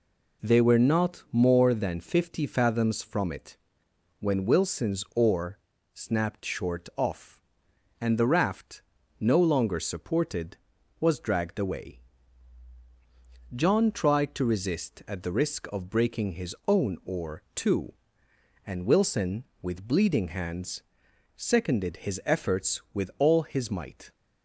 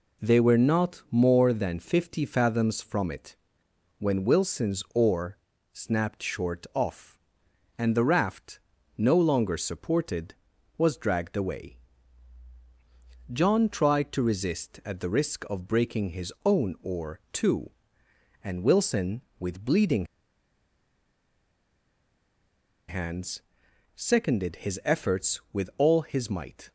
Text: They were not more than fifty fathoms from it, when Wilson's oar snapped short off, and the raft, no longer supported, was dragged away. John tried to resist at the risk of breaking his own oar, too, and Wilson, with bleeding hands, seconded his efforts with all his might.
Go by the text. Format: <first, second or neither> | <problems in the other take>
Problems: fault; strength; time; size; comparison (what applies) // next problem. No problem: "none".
first | pauses between "oar" and "snapped"; slight; at 5.3 s; 0.36 s long; slight in the first // pauses between "bleeding" and "hands"; strong; at 20.0 s; 2.8 s long